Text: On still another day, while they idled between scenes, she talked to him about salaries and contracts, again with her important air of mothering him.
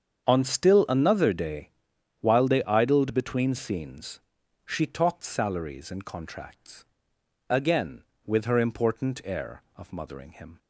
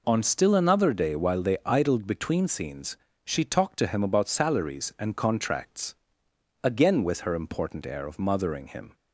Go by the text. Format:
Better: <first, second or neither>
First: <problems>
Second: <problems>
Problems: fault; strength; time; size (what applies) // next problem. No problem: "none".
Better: second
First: starts louder than the rest; strong; until 1.2 s; 7.5 dB // skips "to him about"; at 5.2 s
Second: none